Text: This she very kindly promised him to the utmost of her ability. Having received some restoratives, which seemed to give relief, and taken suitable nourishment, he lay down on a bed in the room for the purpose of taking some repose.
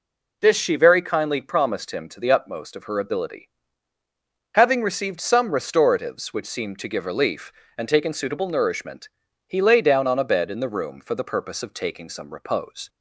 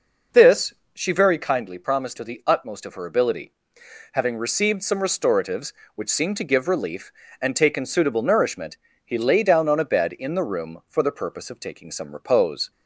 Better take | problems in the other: first | pauses between "This" and "she"; slight; at 0.7 s; 0.20 s long // skips "him"; at 2.1 s

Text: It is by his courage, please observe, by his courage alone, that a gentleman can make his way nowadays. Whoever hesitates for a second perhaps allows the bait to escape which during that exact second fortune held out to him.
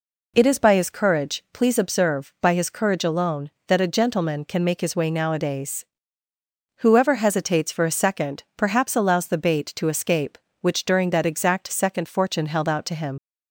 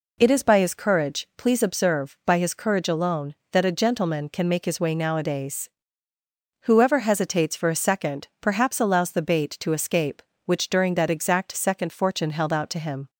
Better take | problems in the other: second | leaves "him" unfinished; at 13.1 s; 75 ms

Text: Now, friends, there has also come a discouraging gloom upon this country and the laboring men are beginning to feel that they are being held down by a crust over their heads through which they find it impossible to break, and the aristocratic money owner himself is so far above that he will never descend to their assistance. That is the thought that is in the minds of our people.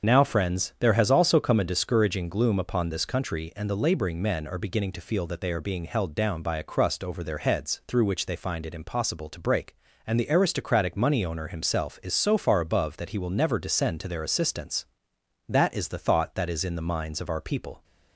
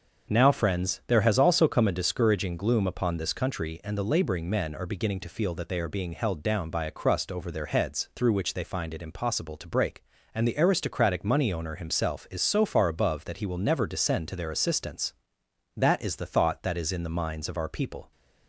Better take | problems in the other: second | loses the start of "Now"; at 0.0 s; 30 ms // starts louder than the rest; until 1.1 s; 6.5 dB; also in the second

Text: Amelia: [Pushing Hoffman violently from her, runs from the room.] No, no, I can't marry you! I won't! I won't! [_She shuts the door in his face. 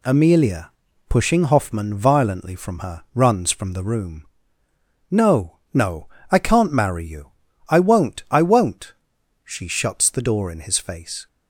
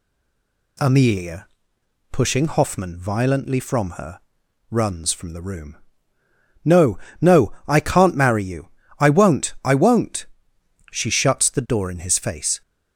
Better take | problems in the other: first | stays silent before the first word; slight; until 0.7 s; 0.7 s long

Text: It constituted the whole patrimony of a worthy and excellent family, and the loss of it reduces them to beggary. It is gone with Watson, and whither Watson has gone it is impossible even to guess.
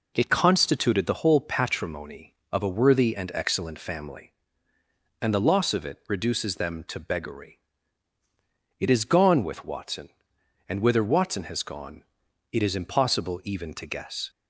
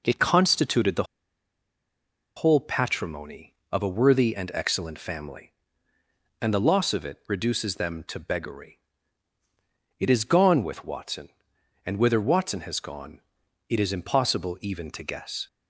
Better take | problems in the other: first | pauses between "the" and "whole"; strong; at 1.0 s; 1.3 s long // pauses between "gone" and "it"; noticeable; at 13.1 s; 0.50 s long; noticeable in the first

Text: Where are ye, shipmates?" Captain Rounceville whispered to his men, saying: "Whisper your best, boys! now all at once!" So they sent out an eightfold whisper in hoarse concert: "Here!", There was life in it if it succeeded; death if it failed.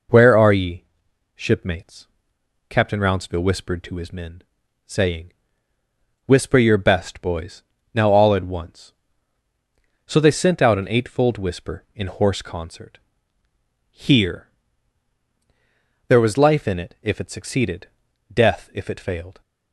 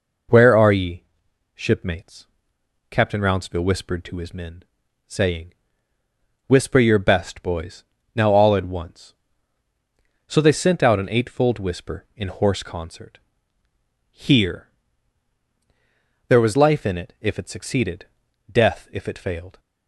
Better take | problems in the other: neither | none

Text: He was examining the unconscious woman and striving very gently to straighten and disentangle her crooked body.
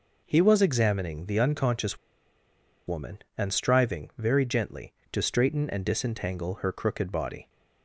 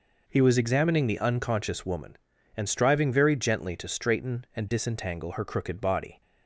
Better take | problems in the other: second | pauses between "unconscious" and "woman"; noticeable; at 1.9 s; 0.89 s long

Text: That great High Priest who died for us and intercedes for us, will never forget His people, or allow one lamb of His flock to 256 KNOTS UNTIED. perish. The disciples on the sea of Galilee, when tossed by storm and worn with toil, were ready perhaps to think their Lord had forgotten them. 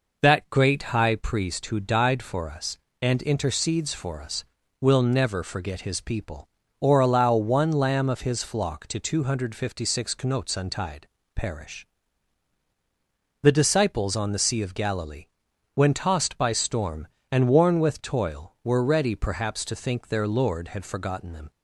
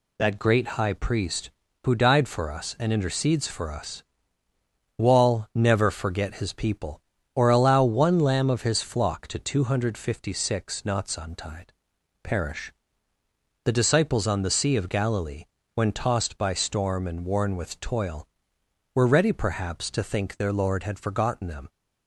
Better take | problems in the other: first | says "wall" for "will"; at 4.9 s

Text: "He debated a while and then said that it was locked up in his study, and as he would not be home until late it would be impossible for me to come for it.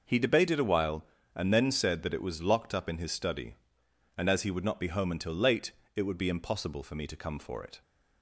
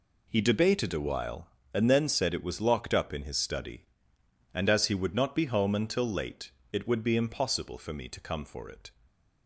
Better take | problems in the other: first | skips "that"; at 2.3 s // pauses between "late" and "it"; slight; at 6.5 s; 0.20 s long; slight in the first

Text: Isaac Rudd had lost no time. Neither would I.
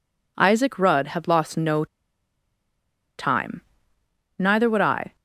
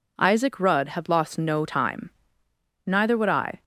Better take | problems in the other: second | pauses between "no" and "time"; strong; at 1.8 s; 1.3 s long

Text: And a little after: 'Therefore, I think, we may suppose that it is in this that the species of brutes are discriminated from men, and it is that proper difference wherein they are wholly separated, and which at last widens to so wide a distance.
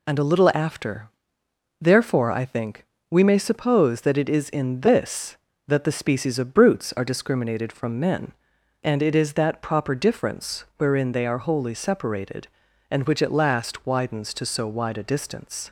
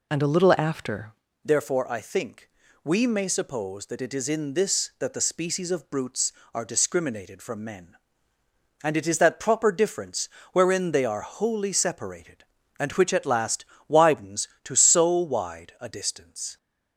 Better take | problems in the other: first | changes voice at "Therefore"; from 1.4 s on; 15.1 s long // pauses between "difference" and "wherein"; slight; at 10.2 s; 0.24 s long // pauses between "last" and "widens"; slight; at 13.6 s; 0.22 s long

